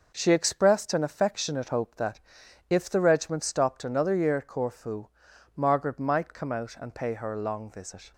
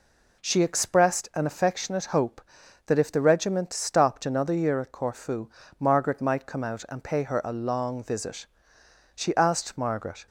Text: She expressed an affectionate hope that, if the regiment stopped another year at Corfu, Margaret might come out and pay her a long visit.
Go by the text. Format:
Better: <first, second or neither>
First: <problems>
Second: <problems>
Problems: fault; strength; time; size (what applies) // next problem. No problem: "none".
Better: first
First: none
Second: goes on to say "She asked Margaret"; noticeable; from 9.1 s on; 1.1 s long